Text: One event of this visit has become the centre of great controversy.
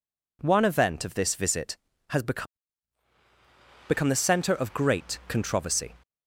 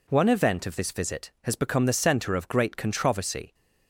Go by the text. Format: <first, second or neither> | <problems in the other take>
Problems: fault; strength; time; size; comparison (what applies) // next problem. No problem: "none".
second | says "become" twice; at 3.8 s